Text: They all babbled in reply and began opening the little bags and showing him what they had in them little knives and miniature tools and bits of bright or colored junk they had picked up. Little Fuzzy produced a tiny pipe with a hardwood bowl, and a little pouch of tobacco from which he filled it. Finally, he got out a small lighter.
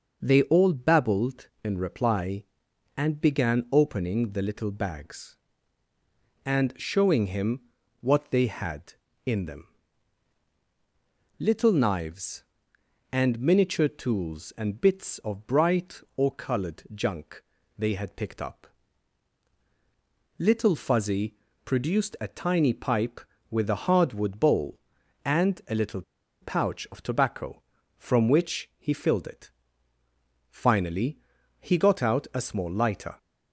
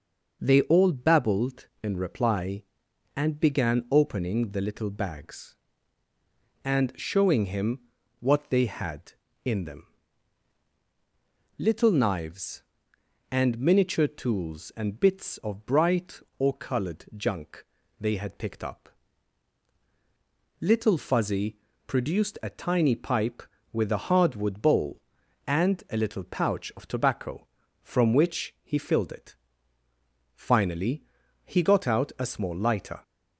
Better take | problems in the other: second | pauses between "him" and "what"; at 7.6 s; 0.40 s long; also in the second // pauses between "them" and "little"; strong; at 9.6 s; 1.7 s long; strong in the second // pauses between "junk" and "they"; slight; at 17.4 s; 0.36 s long; slight in the second // pauses between "Fuzzy" and "produced"; slight; at 21.3 s; 0.32 s long; slight in the second // pauses between "little" and "pouch"; at 26.0 s; 0.39 s long

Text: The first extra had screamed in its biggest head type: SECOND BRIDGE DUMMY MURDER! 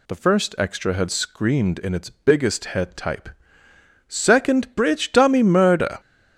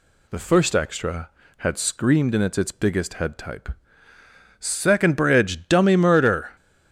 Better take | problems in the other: first | says "its" twice; at 2.5 s

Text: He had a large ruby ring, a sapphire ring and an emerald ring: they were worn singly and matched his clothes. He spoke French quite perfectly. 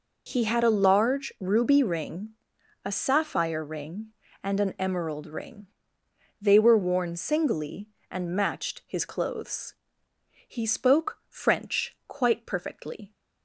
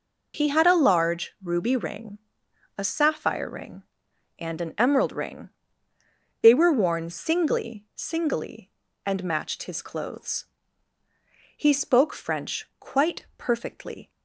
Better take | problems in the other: first | says "singly" twice; at 7.9 s

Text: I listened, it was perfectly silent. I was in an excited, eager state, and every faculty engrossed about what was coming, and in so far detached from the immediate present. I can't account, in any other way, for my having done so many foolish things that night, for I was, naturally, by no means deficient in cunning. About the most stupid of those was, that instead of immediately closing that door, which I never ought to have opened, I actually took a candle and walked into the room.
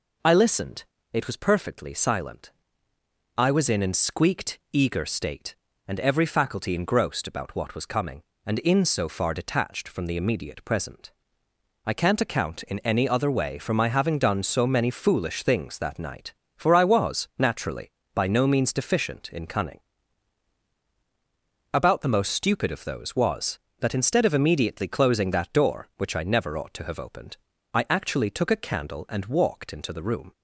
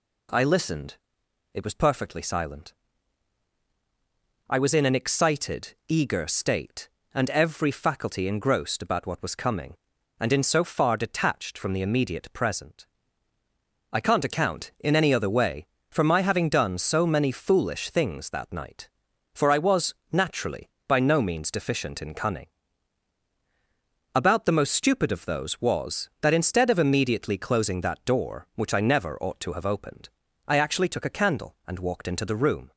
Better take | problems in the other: second | says "squeaked" for "excited"; at 3.9 s

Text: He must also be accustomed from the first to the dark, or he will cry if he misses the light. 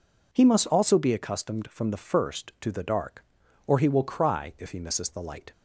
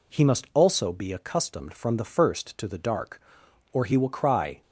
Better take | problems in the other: first | stops before "if he misses the light"; at 4.6 s

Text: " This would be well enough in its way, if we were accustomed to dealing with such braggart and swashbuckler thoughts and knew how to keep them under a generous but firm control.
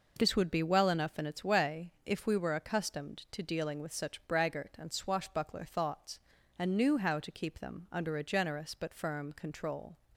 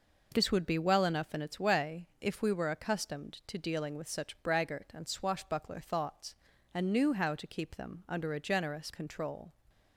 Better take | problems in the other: first | skips "but firm"; at 8.9 s

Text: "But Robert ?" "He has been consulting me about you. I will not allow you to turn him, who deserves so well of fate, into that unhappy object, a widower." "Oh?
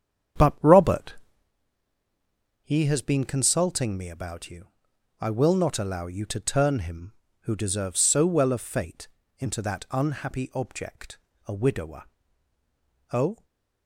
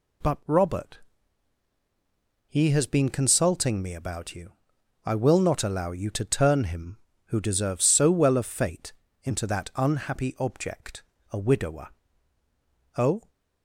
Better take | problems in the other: second | starts louder than the rest; strong; until 1.6 s; 8 dB // stays silent after the last word; slight; from 13.3 s on; 0.5 s long

